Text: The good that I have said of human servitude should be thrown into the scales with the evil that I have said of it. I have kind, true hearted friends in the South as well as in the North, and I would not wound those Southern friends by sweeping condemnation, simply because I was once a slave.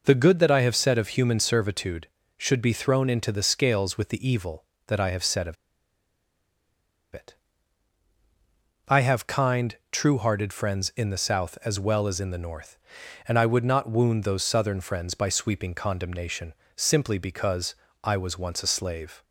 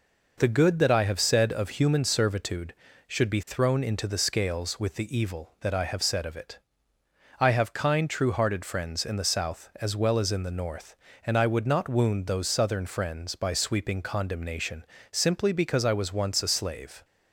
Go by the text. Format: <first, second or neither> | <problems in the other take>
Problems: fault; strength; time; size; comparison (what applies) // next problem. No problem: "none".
second | pauses between "of" and "it"; strong; at 5.5 s; 1.5 s long // pauses between "because" and "I"; slight; at 17.7 s; 0.30 s long